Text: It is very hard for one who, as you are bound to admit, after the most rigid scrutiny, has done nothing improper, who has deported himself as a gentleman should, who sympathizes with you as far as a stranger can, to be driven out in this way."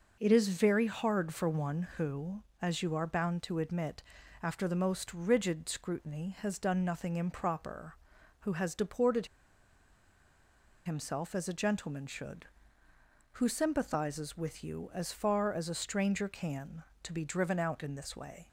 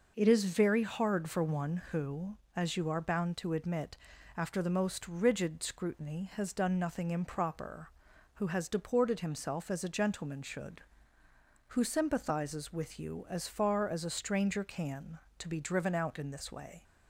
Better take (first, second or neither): second